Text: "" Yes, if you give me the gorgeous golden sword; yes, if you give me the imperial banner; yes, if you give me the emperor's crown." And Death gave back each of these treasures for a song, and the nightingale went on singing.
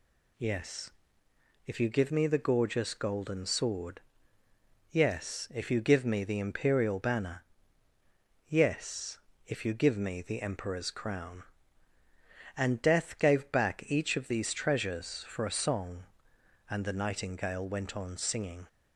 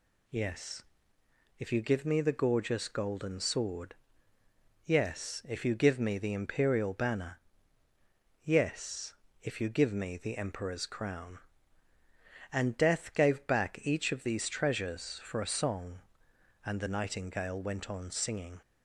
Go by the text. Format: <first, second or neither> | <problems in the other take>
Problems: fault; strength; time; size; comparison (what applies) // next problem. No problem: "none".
neither | none